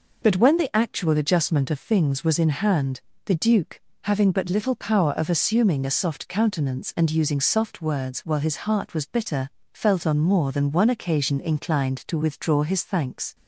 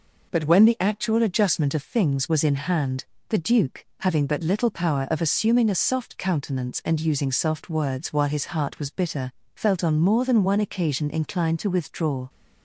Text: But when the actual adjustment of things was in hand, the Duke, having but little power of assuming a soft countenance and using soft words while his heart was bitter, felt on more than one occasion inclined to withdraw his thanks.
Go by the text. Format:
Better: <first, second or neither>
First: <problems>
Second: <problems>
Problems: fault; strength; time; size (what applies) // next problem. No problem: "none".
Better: first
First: none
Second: stops before "his thanks"; at 12.2 s